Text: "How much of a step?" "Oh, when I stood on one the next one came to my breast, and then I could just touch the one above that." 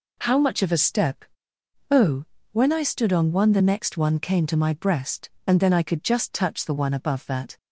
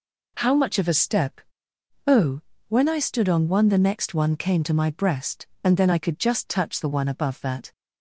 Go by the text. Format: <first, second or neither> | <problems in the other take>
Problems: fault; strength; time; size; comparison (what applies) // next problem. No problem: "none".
neither | none